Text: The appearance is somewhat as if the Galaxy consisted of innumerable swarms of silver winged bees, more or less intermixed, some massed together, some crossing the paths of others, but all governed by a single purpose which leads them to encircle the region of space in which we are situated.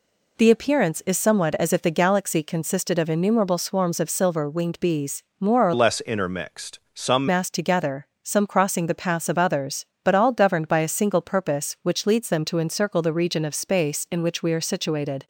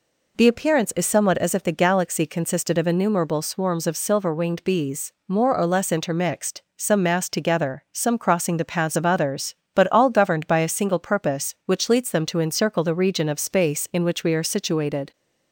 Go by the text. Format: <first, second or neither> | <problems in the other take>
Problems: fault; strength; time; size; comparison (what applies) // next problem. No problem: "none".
second | changes voice from "less" to "some"; from 5.7 to 7.2 s; 1.5 s long